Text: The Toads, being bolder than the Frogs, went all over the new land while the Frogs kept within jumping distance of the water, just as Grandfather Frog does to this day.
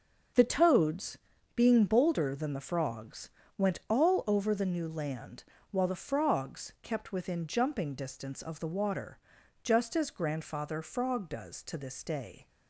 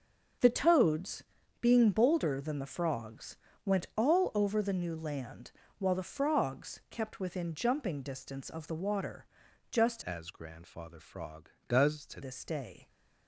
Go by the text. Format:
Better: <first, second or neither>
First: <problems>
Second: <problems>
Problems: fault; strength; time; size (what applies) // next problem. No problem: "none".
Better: first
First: starts louder than the rest; until 1.7 s; 6 dB // pauses between "land" and "while"; slight; at 5.4 s; 0.28 s long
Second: starts louder than the rest; until 1.7 s; 6 dB // pauses between "land" and "while"; slight; at 5.5 s; 0.28 s long // changes voice from "as" to "to"; from 10.0 to 12.2 s; 2.2 s long